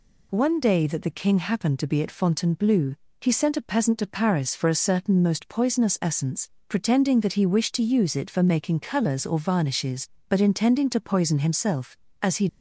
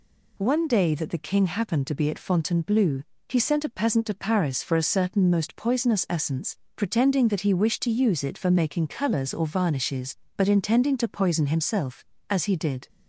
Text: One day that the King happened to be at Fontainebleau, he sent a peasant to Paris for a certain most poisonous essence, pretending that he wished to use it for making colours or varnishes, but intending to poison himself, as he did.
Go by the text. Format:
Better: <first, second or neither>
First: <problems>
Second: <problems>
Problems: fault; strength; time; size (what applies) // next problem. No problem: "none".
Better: second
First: stops before "did"; at 12.4 s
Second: none